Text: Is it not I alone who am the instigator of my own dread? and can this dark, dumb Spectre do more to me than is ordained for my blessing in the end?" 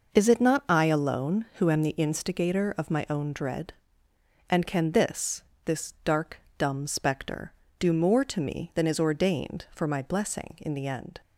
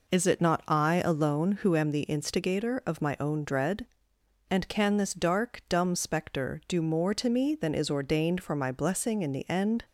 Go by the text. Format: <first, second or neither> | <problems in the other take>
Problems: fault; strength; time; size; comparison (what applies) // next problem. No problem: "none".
second | says "this" twice; at 5.6 s